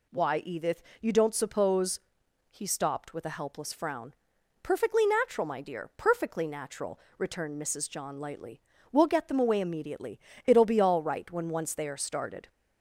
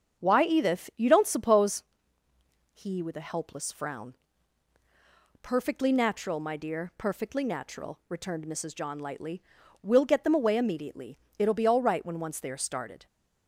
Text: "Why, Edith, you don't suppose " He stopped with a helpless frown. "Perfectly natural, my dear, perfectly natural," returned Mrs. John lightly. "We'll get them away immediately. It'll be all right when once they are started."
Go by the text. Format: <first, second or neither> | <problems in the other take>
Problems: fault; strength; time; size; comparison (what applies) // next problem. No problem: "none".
first | starts louder than the rest; strong; until 1.2 s; 7 dB // skips "stopped"; at 3.0 s